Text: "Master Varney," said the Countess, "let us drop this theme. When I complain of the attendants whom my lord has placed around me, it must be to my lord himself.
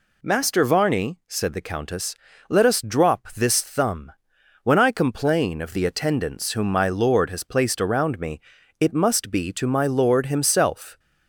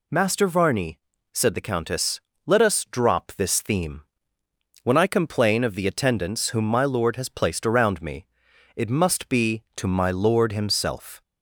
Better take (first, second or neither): second